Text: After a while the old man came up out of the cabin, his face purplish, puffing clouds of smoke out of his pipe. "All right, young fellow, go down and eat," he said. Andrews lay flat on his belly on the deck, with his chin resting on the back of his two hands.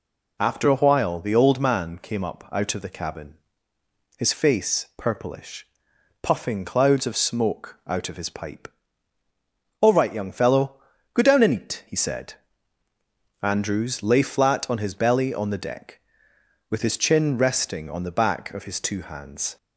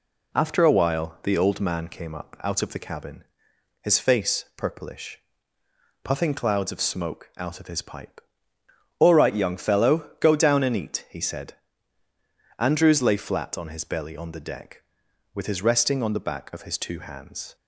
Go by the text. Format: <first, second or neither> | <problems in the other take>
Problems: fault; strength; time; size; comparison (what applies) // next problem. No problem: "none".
first | skips "chin"; at 15.6 s